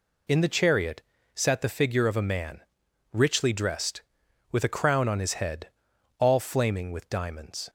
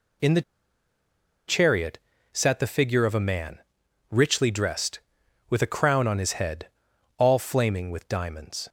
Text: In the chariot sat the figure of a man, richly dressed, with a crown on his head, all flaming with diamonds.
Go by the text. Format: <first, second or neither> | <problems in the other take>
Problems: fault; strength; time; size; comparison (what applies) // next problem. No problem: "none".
first | pauses between "the" and "chariot"; at 0.4 s; 1.0 s long // pauses between "chariot" and "sat"; slight; at 1.9 s; 0.34 s long; slight in the first